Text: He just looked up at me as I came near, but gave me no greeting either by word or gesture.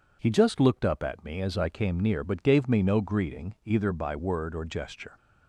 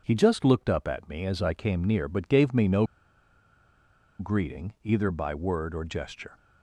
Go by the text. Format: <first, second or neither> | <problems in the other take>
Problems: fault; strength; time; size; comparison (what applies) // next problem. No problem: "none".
first | pauses between "no" and "greeting"; strong; at 2.8 s; 1.3 s long